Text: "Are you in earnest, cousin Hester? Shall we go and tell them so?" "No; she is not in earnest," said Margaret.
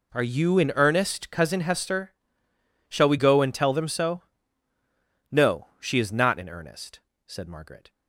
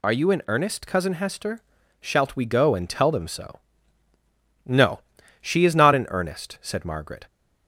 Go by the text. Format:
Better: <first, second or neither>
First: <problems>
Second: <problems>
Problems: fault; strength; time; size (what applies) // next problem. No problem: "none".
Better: first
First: none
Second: says "Shalt" for "Shall"; at 2.0 s